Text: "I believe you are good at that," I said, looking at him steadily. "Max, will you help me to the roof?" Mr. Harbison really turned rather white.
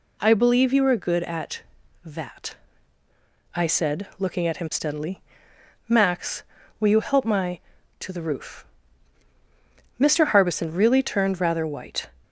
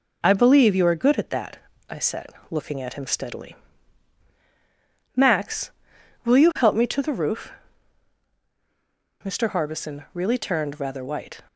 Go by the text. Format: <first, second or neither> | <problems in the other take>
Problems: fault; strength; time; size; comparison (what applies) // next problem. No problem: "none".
second | says "my" for "me"; at 7.2 s